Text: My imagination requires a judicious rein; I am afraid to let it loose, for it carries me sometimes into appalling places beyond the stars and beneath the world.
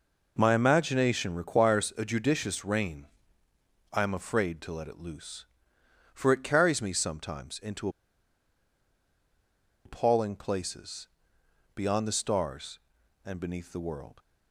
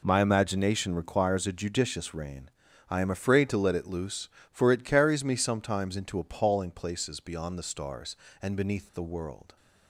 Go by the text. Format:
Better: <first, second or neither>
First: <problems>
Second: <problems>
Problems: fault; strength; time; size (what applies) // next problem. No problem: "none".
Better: second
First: pauses between "into" and "appalling"; strong; at 7.8 s; 1.9 s long // pauses between "places" and "beyond"; noticeable; at 11.0 s; 0.66 s long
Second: none